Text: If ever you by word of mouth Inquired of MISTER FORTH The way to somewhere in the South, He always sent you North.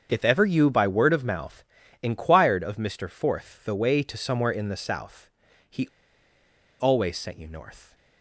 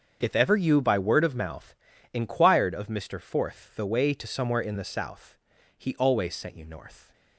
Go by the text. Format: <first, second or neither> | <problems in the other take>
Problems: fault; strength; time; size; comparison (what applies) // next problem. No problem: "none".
second | starts louder than the rest; until 1.1 s; 7 dB; also in the second // pauses between "mouth" and "Inquired"; at 1.6 s; 0.40 s long; also in the second // pauses between "He" and "always"; noticeable; at 5.8 s; 0.93 s long